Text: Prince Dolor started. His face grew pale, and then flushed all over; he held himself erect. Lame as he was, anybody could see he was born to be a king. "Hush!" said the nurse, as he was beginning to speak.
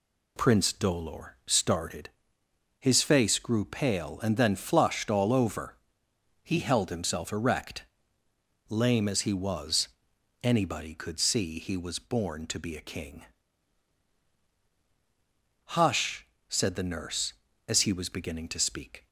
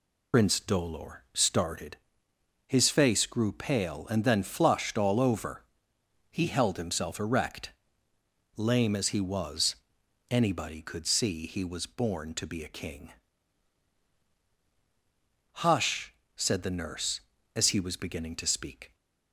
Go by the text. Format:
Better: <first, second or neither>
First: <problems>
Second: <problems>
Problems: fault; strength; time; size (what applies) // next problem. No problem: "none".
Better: first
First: none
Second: loses the start of "Prince"; at 0.3 s; 105 ms